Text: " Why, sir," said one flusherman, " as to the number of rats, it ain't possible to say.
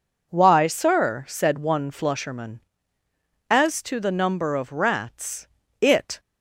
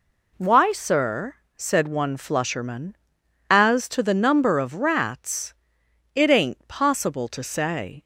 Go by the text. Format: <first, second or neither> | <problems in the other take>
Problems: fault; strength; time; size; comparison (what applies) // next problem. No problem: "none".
second | stops before "ain't possible to say"; at 6.1 s